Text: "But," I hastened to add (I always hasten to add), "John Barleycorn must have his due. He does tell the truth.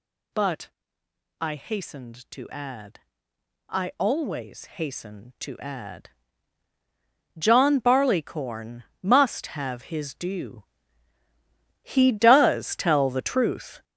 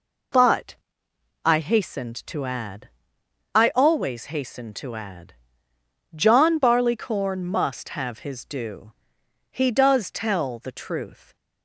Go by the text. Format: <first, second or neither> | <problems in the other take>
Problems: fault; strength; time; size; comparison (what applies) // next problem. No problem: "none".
second | gets louder; strong; throughout; 9 dB // pauses between "Barleycorn" and "must"; slight; at 8.8 s; 0.20 s long